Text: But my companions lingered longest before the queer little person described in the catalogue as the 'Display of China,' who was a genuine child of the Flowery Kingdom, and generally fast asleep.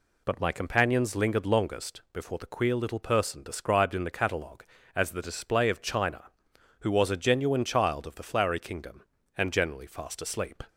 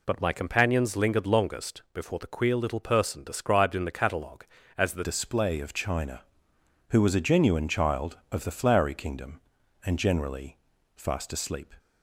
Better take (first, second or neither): first